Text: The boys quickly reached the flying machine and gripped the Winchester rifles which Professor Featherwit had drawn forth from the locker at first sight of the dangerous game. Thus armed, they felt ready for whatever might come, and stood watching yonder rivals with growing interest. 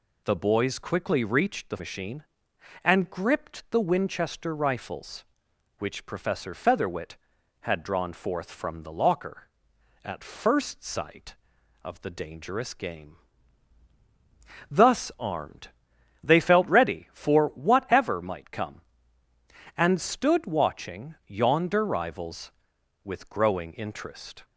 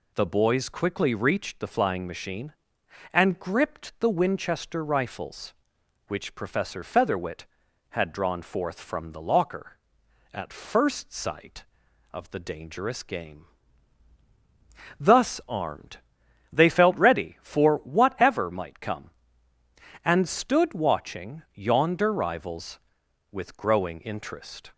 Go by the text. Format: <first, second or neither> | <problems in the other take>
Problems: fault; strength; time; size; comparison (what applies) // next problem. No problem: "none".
second | skips "flying"; at 1.7 s